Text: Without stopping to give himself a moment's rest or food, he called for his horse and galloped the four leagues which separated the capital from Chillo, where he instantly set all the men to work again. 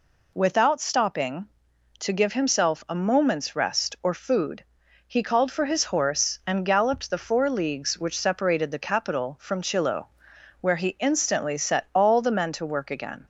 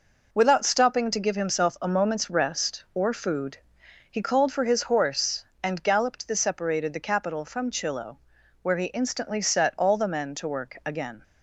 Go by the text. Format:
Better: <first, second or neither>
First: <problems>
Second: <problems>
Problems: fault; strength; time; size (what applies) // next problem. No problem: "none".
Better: first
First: none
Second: skips "four leagues which"; at 6.3 s